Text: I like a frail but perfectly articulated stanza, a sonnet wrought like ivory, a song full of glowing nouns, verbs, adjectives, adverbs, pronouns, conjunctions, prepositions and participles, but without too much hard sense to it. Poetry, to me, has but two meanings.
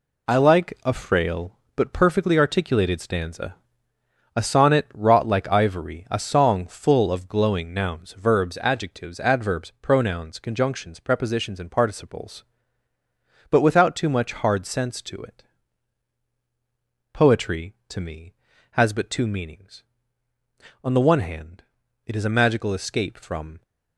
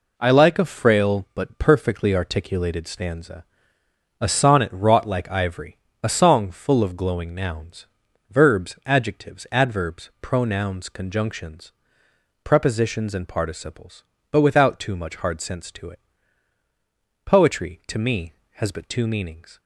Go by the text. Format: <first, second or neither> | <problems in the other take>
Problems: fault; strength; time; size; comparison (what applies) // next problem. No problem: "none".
second | goes on to say "On the one hand it is a magical escape from"; strong; from 20.8 s on; 2.7 s long